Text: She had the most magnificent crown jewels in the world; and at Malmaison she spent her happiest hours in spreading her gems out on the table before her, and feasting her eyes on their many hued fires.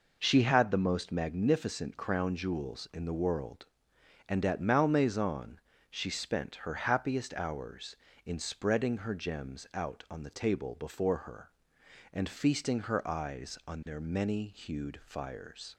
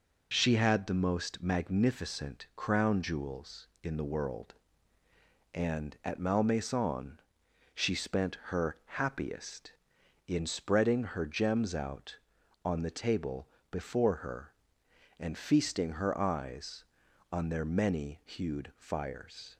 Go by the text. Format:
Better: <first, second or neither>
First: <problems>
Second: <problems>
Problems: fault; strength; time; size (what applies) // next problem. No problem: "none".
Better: first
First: pauses between "Malmaison" and "she"; slight; at 5.6 s; 0.28 s long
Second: pauses between "Malmaison" and "she"; noticeable; at 7.1 s; 0.56 s long // pauses between "spent" and "her"; slight; at 8.3 s; 0.18 s long // skips "hours"; at 10.0 s // pauses between "table" and "before"; slight; at 13.4 s; 0.22 s long